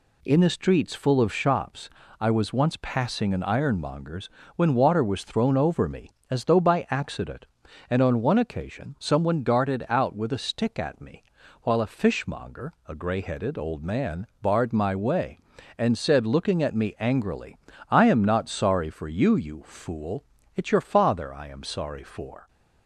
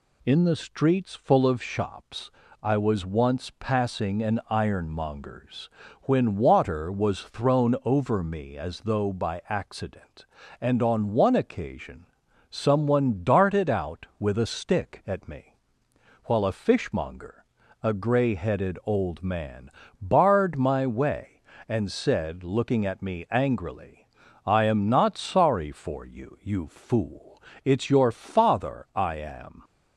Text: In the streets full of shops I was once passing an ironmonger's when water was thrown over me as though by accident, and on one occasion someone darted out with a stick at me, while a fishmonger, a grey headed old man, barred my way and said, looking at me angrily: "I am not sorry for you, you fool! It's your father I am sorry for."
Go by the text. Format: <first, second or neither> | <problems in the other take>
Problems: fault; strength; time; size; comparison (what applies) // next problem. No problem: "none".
first | pauses between "shops" and "I"; slight; at 2.2 s; 0.32 s long; slight in the first // pauses between "ironmonger's" and "when"; slight; at 5.6 s; 0.32 s long; slight in the first // pauses between "occasion" and "someone"; noticeable; at 12.0 s; 0.46 s long // stops before "sorry for"; at 29.6 s